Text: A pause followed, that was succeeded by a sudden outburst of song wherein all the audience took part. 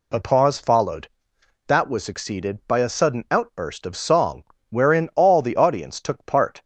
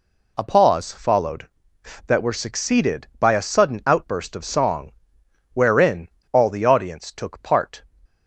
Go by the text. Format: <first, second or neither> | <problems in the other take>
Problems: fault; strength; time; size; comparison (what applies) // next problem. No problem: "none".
first | says "were" for "was"; at 2.2 s // pauses between "song" and "wherein"; noticeable; at 4.9 s; 0.62 s long; slight in the first // pauses between "wherein" and "all"; slight; at 6.0 s; 0.23 s long